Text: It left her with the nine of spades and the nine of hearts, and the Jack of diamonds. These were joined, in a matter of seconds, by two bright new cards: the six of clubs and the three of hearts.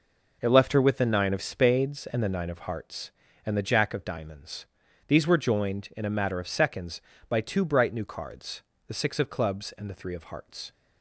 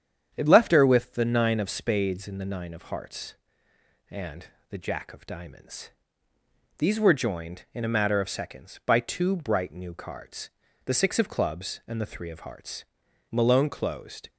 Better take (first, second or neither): first